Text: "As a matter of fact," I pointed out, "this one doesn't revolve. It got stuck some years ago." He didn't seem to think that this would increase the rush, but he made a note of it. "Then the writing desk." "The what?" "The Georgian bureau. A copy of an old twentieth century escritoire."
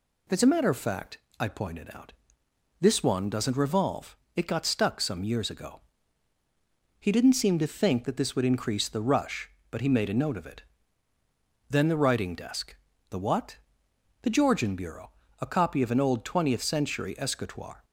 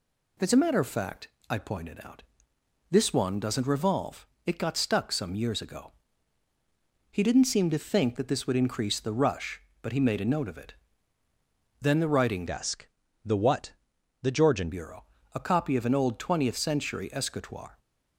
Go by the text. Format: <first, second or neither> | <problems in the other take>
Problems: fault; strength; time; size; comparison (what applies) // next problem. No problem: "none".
first | changes voice from "desk" to "Georgian"; from 12.4 to 14.7 s; 2.3 s long